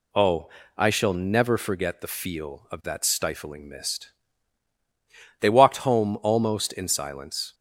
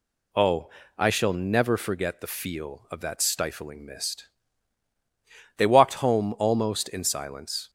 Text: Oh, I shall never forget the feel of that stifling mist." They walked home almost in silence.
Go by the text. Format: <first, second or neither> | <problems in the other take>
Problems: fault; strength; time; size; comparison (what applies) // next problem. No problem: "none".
neither | none